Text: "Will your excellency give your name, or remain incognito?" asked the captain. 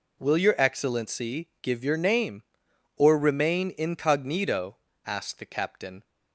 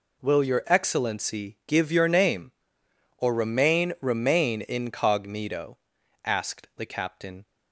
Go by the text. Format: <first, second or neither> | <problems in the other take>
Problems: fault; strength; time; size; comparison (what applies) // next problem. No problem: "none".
first | says "remain" twice; at 4.0 s